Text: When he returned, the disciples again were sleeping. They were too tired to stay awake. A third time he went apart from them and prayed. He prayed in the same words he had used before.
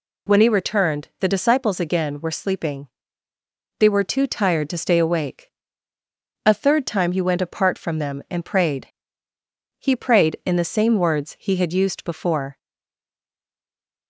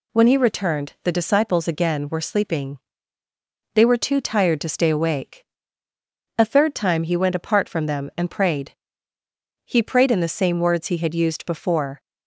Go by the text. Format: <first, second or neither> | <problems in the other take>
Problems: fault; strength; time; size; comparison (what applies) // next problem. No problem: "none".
second | stays silent after the last word; noticeable; from 12.5 s on; 1.5 s long